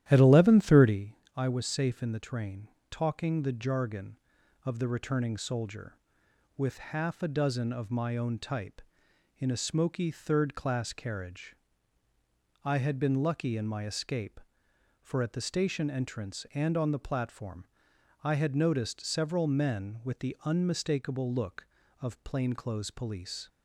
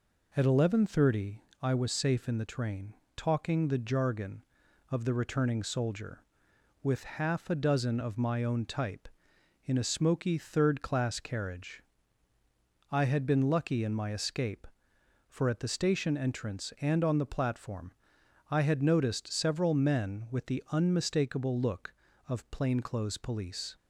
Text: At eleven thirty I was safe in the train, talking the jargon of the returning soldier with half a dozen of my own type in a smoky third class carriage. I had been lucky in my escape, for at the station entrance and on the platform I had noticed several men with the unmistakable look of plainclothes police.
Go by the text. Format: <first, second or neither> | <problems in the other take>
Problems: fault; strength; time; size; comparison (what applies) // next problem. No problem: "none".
second | starts louder than the rest; strong; until 1.0 s; 12 dB // pauses between "thirty" and "I"; slight; at 1.1 s; 0.20 s long; slight in the second // pauses between "platform" and "I"; noticeable; at 17.6 s; 0.62 s long; noticeable in the second